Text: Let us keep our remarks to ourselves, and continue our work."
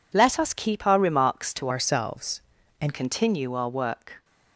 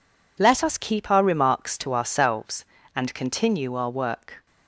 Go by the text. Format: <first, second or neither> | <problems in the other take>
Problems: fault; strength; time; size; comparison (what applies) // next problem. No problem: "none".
second | changes voice from "ourselves" to "and"; from 1.6 to 2.9 s; 1.3 s long